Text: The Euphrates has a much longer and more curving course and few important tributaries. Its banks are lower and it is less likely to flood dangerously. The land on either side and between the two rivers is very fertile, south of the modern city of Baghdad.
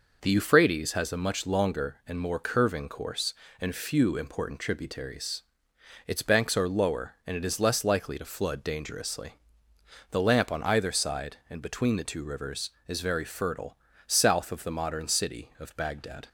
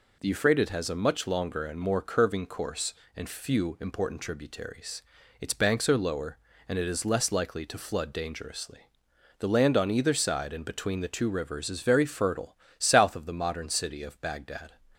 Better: second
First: says "lamp" for "land"; at 10.1 s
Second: none

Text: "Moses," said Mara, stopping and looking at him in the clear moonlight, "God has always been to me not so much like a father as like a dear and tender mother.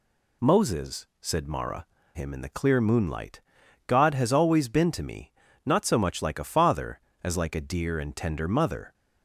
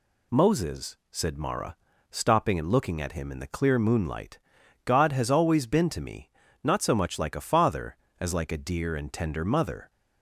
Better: second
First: skips "stopping and looking at"; at 2.0 s // pauses between "me" and "not"; slight; at 5.3 s; 0.34 s long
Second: pauses between "me" and "not"; slight; at 6.2 s; 0.34 s long

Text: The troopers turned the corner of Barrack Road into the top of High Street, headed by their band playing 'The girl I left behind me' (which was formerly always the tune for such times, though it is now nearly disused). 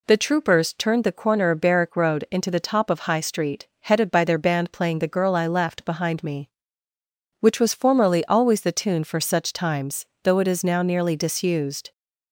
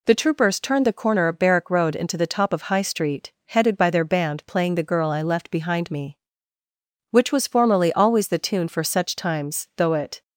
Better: first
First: none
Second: stops before "is now nearly disused"; at 10.2 s

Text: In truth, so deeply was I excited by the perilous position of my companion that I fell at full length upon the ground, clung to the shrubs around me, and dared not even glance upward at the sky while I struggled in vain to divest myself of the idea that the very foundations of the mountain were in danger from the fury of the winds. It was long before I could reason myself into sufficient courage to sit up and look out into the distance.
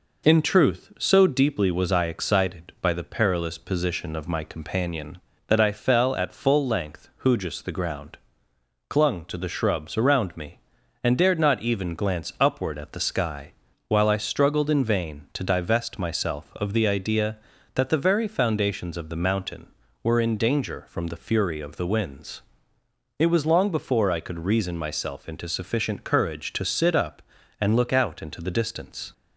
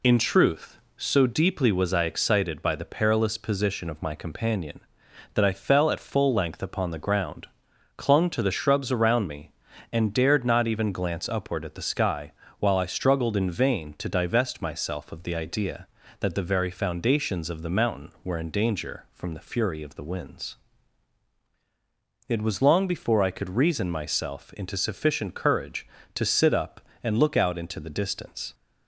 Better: second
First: says "hujus" for "upon"; at 7.2 s // pauses between "sky" and "while"; slight; at 13.5 s; 0.36 s long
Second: pauses between "sky" and "while"; slight; at 12.3 s; 0.28 s long

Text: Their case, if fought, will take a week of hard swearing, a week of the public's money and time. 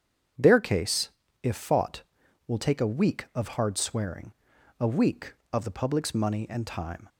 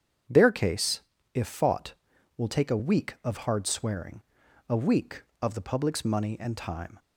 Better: neither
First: starts louder than the rest; strong; until 1.7 s; 8 dB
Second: starts louder than the rest; strong; until 1.6 s; 8 dB

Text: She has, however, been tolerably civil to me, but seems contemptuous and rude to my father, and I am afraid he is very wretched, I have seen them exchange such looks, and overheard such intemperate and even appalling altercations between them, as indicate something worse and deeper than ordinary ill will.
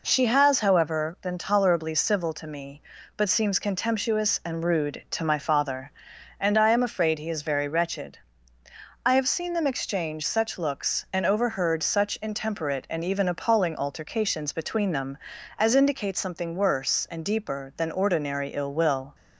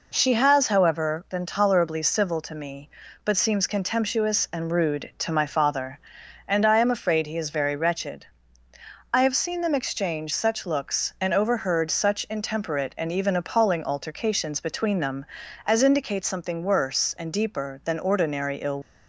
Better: first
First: none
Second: stops before "will"; at 18.8 s

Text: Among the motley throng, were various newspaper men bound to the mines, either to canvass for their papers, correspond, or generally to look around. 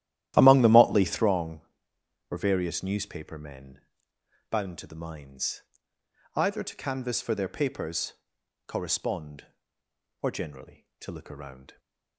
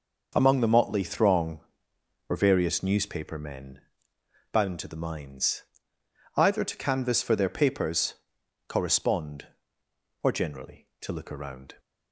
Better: second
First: starts louder than the rest; strong; until 1.3 s; 13 dB // pauses between "men" and "bound"; noticeable; at 3.8 s; 0.68 s long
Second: pauses between "men" and "bound"; noticeable; at 3.8 s; 0.70 s long

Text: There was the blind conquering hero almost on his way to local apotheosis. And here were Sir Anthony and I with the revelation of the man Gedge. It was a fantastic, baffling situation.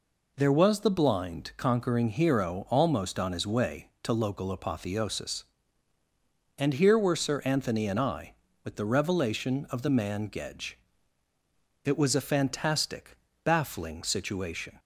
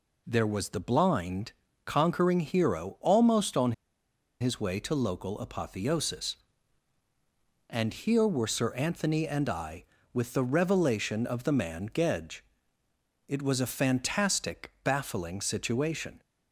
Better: first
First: none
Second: pauses between "blind" and "conquering"; slight; at 1.5 s; 0.32 s long // pauses between "on" and "his"; noticeable; at 3.7 s; 0.67 s long

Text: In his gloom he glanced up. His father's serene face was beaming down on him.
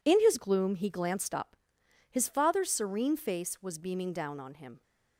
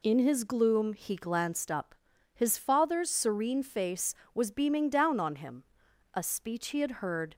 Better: first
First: none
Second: goes on to say "A speech he had heard"; noticeable; from 6.1 s on; 1.2 s long

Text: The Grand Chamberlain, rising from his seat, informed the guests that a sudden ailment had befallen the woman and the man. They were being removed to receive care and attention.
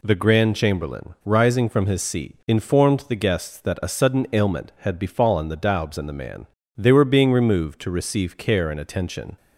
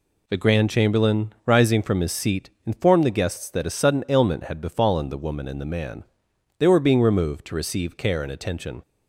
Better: second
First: says "daubs" for "woman"; at 5.5 s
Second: none

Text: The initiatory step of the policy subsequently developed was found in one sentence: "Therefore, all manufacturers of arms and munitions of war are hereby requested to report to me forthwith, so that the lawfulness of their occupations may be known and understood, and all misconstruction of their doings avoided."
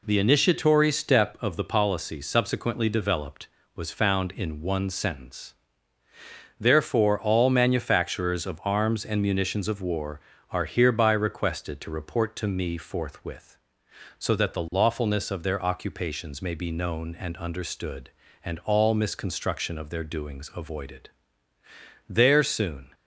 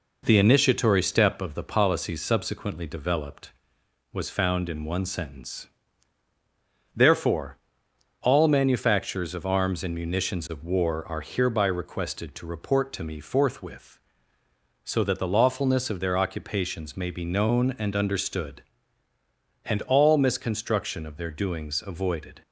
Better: second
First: goes on to say "There soon"; noticeable; from 22.0 s on; 0.86 s long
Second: none

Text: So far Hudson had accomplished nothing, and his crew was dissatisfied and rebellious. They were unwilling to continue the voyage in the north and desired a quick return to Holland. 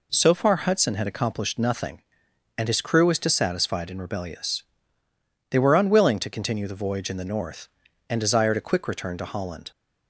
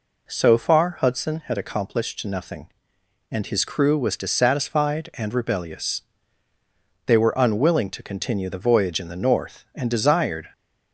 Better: first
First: none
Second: stops before "a quick return to Holland"; at 10.5 s

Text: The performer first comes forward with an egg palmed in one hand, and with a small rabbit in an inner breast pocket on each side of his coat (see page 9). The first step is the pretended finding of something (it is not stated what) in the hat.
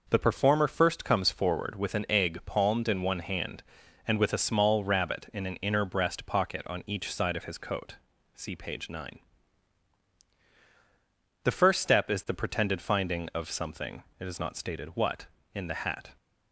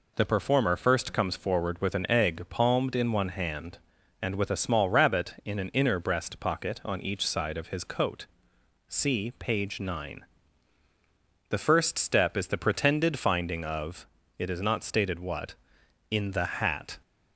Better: first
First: none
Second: skips "something"; at 14.2 s

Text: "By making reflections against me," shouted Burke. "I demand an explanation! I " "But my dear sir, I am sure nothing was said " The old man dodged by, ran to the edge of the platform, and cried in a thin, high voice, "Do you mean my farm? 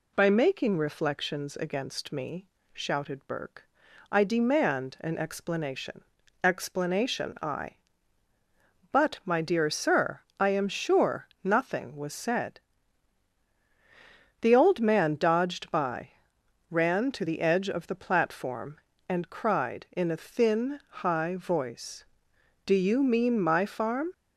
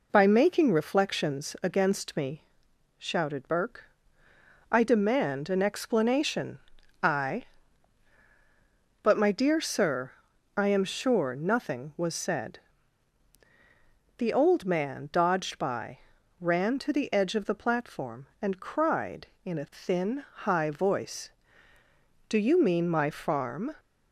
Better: second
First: says "explanation" twice; at 6.4 s // pauses between "sure" and "nothing"; slight; at 11.2 s; 0.16 s long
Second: none

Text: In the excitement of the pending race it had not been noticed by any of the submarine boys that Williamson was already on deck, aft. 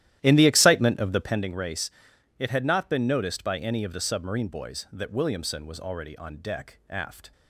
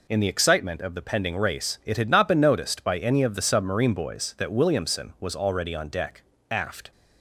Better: second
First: starts louder than the rest; strong; until 1.4 s; 13 dB // pauses between "race" and "it"; noticeable; at 1.8 s; 0.48 s long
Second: none

